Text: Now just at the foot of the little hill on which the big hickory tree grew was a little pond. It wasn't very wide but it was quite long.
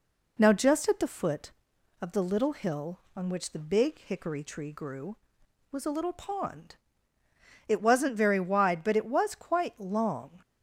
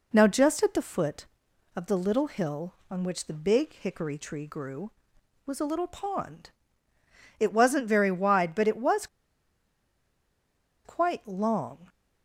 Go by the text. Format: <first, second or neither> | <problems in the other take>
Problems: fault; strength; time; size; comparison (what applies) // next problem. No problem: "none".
first | pauses between "was" and "quite"; strong; at 9.0 s; 1.7 s long